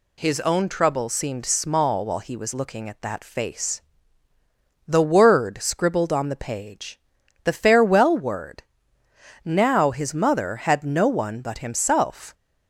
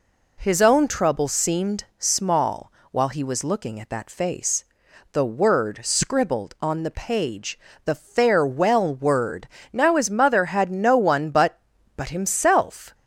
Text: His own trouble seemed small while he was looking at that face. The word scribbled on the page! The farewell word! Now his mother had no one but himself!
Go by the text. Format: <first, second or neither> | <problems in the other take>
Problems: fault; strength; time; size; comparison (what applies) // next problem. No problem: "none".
first | pauses between "seemed" and "small"; slight; at 1.8 s; 0.16 s long // pauses between "small" and "while"; slight; at 2.7 s; 0.22 s long // says "but" twice; at 11.9 s